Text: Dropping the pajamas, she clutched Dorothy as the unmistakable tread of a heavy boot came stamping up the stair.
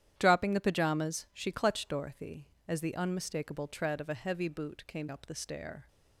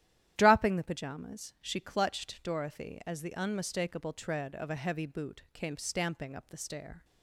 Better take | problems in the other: second | starts louder than the rest; strong; until 1.1 s; 10.5 dB; strong in the second // skips "stamping"; at 5.0 s

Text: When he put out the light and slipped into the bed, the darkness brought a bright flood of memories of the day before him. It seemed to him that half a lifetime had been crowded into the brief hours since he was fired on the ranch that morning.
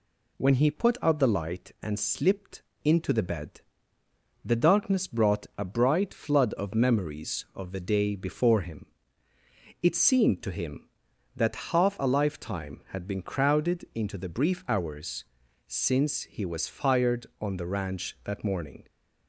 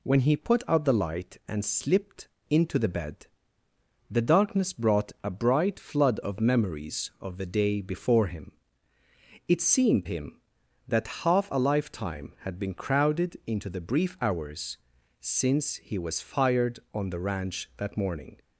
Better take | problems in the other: first | pauses between "slipped" and "into"; slight; at 2.2 s; 0.20 s long; slight in the first // skips "to"; at 10.0 s // pauses between "hours" and "since"; at 14.7 s; 0.44 s long; also in the first

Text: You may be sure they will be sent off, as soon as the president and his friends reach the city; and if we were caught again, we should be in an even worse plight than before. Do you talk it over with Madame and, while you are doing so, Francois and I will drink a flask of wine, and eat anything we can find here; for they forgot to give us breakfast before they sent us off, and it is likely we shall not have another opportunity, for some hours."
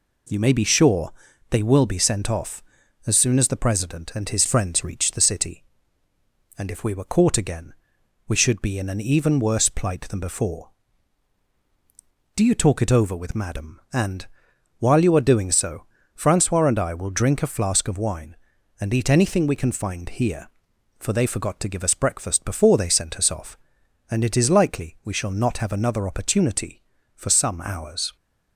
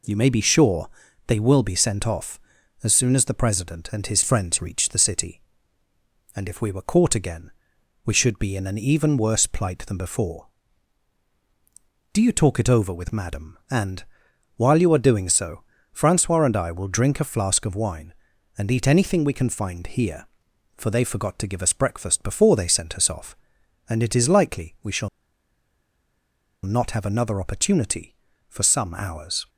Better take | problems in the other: first | pauses between "sure" and "they"; at 0.8 s; 0.38 s long; also in the first // pauses between "shall" and "not"; strong; at 25.0 s; 1.5 s long

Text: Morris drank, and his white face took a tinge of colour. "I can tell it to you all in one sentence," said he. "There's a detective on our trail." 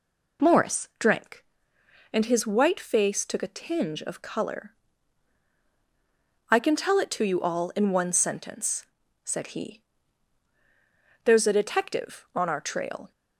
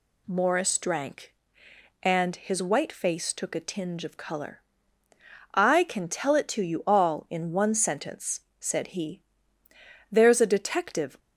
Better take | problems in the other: first | stops before "on our trail"; at 11.1 s

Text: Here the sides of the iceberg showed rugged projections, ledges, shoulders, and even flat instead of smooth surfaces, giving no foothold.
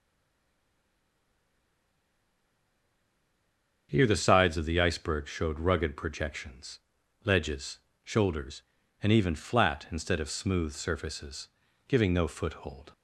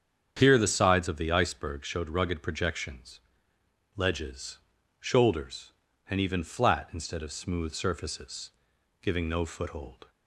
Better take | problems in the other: second | stays silent before the first word; strong; until 3.8 s; 3.8 s long // starts louder than the rest; strong; until 4.9 s; 7.5 dB; strong in the second

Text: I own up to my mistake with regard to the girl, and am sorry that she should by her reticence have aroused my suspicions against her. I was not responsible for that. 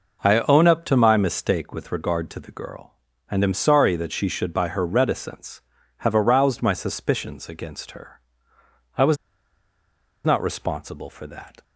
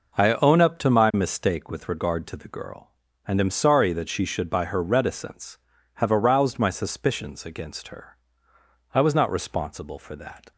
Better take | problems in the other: second | pauses between "was" and "not"; at 9.1 s; 1.0 s long

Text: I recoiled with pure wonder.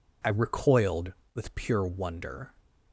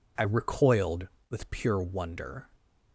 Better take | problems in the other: neither | none

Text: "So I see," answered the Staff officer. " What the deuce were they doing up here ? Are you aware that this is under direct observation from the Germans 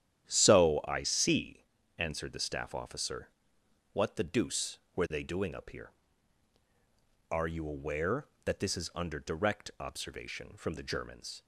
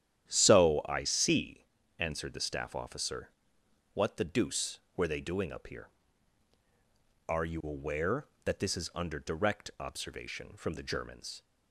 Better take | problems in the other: neither | starts louder than the rest; strong; the same in both

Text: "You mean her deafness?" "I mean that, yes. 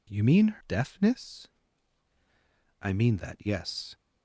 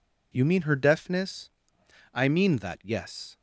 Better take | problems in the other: second | skips "her"; at 0.6 s

